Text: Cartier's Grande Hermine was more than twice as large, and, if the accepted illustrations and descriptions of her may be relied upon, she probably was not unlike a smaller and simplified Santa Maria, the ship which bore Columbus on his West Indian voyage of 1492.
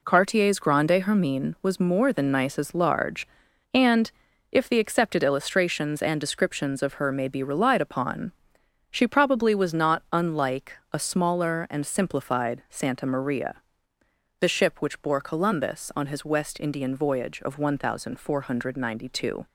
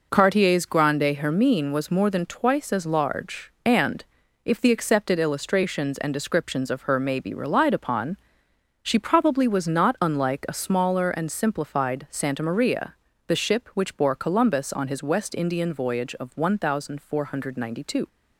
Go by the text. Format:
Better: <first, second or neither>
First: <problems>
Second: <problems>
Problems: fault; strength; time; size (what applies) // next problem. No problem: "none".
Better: second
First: says "nice" for "twice"; at 2.3 s // pauses between "unlike" and "a"; slight; at 10.7 s; 0.18 s long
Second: none